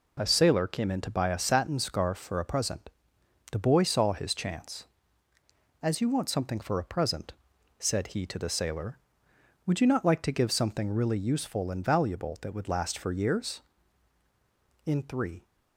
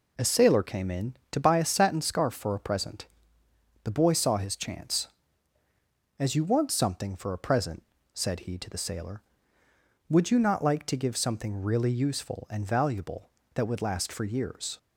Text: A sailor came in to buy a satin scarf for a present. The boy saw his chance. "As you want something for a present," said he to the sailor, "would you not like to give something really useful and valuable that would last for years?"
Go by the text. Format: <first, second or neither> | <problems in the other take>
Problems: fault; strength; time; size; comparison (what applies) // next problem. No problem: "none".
second | goes on to say "In three"; from 14.8 s on; 0.60 s long